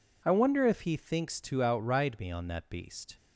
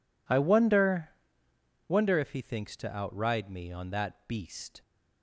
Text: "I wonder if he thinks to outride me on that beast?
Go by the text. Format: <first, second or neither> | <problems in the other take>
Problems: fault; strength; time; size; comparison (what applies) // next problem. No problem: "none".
first | says "wonder" twice; at 1.8 s